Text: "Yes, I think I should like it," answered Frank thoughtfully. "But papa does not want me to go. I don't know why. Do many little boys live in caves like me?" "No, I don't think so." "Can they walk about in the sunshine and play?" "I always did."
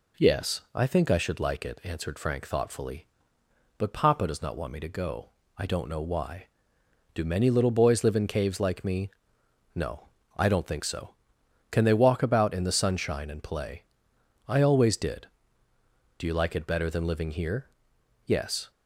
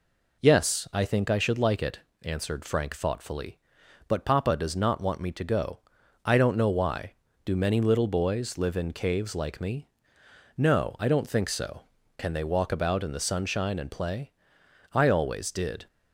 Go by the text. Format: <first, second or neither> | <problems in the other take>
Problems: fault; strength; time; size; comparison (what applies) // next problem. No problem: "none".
second | goes on to say "Do you like it better than living here Yes"; strong; from 16.1 s on; 2.5 s long